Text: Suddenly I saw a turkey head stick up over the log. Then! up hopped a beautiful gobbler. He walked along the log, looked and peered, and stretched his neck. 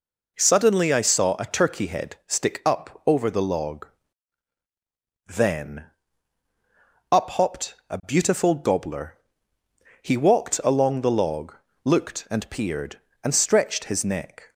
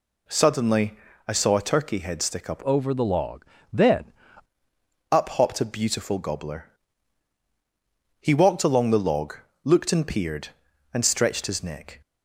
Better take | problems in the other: first | pauses between "Suddenly" and "I"; slight; at 0.9 s; 0.34 s long // changes voice from "over" to "Then"; from 2.6 to 4.1 s; 1.5 s long

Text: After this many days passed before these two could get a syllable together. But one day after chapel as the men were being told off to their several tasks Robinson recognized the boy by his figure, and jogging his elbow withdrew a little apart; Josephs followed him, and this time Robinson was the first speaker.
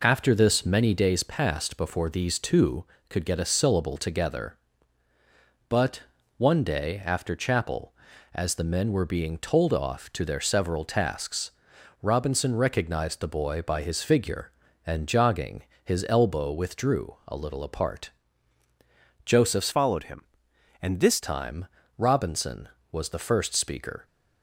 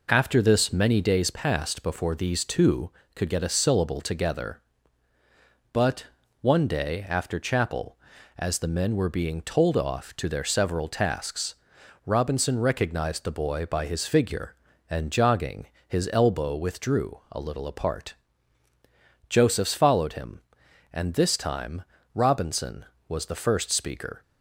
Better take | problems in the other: second | pauses between "But" and "one"; slight; at 6.0 s; 0.36 s long; slight in the second // pauses between "tasks" and "Robinson"; noticeable; at 11.5 s; 0.50 s long; noticeable in the second // pauses between "jogging" and "his"; slight; at 15.6 s; 0.22 s long; slight in the second // changes voice from "followed" to "this"; from 19.7 to 21.2 s; 1.5 s long // pauses between "time" and "Robinson"; slight; at 21.6 s; 0.32 s long; slight in the second

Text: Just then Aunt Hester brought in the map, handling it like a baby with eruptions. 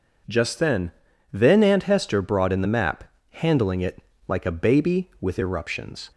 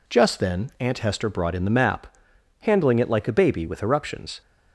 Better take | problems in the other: second | says "then" twice; at 1.3 s // pauses between "it" and "like"; slight; at 4.0 s; 0.24 s long

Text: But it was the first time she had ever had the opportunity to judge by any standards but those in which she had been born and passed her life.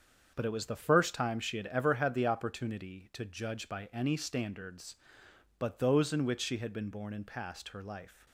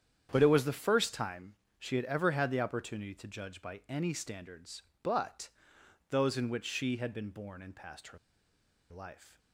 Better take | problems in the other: first | starts louder than the rest; strong; until 1.3 s; 9 dB; strong in the first // pauses between "time" and "she"; slight; at 1.5 s; 0.24 s long // pauses between "but" and "those"; noticeable; at 5.4 s; 0.62 s long // pauses between "her" and "life"; noticeable; at 8.1 s; 0.72 s long

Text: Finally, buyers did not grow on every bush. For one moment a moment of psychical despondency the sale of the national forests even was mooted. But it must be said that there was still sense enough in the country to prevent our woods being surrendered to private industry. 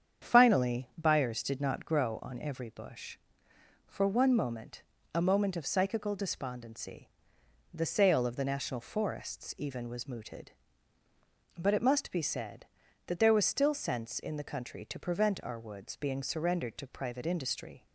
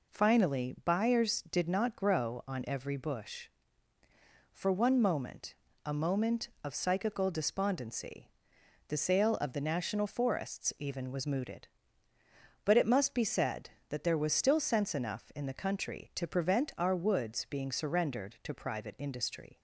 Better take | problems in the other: second | starts louder than the rest; strong; until 1.3 s; 8 dB // pauses between "moment" and "a"; slight; at 4.8 s; 0.32 s long; slight in the second // pauses between "despondency" and "the"; noticeable; at 7.0 s; 0.64 s long; noticeable in the second // skips "enough"; at 14.2 s

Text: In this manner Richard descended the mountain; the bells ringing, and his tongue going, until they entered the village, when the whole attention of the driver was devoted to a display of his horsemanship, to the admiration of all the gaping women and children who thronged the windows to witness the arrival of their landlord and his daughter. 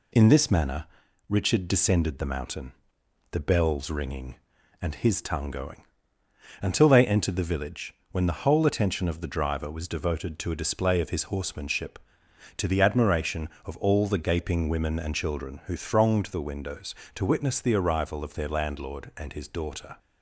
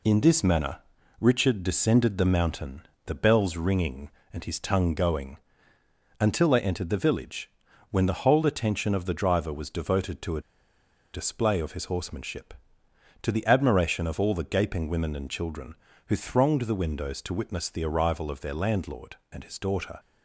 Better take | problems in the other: first | pauses between "manner" and "Richard"; at 0.7 s; 0.42 s long; also in the first // pauses between "a" and "display"; noticeable; at 10.4 s; 0.73 s long

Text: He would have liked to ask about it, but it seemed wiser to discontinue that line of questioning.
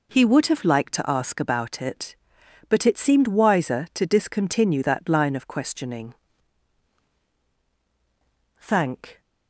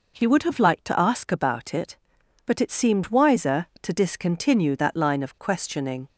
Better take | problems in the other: second | goes on to say "Thank"; noticeable; from 8.5 s on; 0.62 s long

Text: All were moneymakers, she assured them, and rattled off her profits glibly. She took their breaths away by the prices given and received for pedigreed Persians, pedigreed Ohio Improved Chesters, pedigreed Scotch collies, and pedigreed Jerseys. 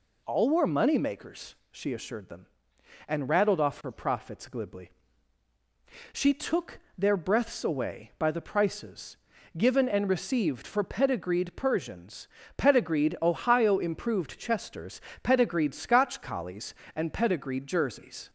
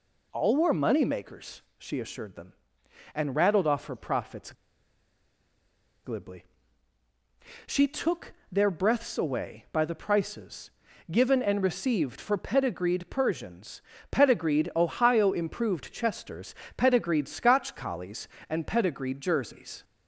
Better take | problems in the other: first | pauses between "profits" and "glibly"; strong; at 4.5 s; 1.5 s long // pauses between "took" and "their"; slight; at 8.3 s; 0.18 s long; slight in the first // pauses between "prices" and "given"; at 10.6 s; 0.40 s long; also in the first

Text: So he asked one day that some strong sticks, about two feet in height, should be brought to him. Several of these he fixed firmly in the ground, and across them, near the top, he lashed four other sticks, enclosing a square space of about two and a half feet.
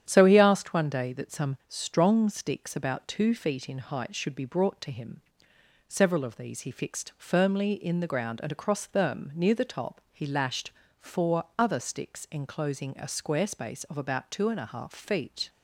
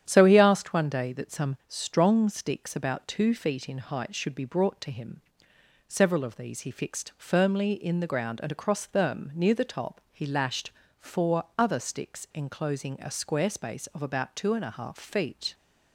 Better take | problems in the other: neither | starts louder than the rest; strong; the same in both // pauses between "lashed" and "four"; slight; the same in both // pauses between "four" and "other"; slight; the same in both

